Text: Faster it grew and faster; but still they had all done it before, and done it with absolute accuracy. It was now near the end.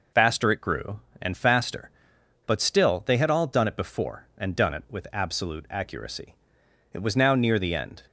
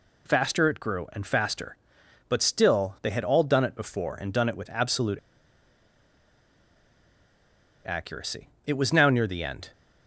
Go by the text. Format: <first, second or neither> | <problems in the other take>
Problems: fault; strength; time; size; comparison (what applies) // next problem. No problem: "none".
first | pauses between "absolute" and "accuracy"; strong; at 5.1 s; 2.6 s long